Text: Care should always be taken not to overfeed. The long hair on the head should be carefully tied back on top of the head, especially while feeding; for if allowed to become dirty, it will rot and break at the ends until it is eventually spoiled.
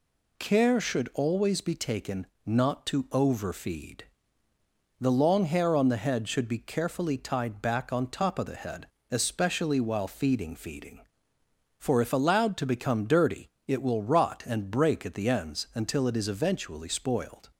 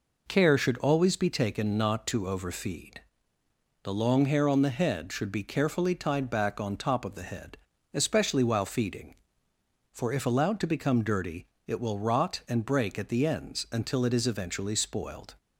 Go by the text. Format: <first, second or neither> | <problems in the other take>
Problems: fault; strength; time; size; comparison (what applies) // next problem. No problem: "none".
second | pauses between "taken" and "not"; slight; at 2.2 s; 0.20 s long // says "feeding" twice; at 10.5 s